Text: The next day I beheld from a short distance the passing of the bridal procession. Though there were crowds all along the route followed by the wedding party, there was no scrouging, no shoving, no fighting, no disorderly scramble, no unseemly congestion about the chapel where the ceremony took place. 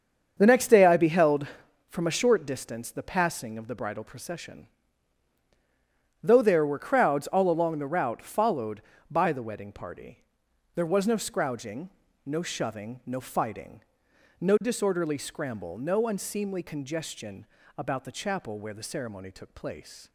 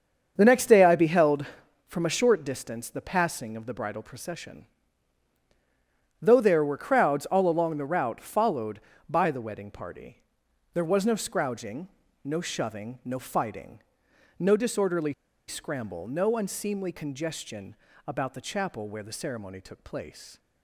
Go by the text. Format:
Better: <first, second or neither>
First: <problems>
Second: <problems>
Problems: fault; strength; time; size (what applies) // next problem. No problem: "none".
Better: first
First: starts louder than the rest; until 1.3 s; 7 dB // pauses between "congestion" and "about"; slight; at 17.4 s; 0.32 s long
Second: starts louder than the rest; until 1.3 s; 7 dB // pauses between "disorderly" and "scramble"; slight; at 15.1 s; 0.34 s long // pauses between "congestion" and "about"; slight; at 17.7 s; 0.32 s long